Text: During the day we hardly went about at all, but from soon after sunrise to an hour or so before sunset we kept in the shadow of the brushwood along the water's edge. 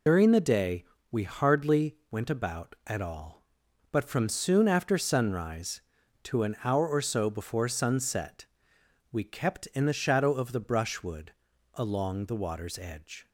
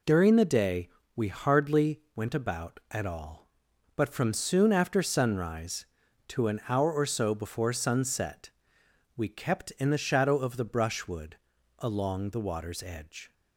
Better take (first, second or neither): second